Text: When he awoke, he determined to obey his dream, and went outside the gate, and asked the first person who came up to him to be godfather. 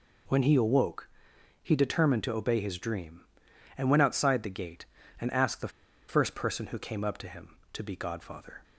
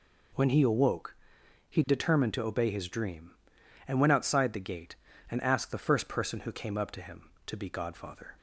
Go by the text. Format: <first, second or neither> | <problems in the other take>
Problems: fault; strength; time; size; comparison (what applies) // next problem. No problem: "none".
second | pauses between "the" and "first"; at 5.6 s; 0.39 s long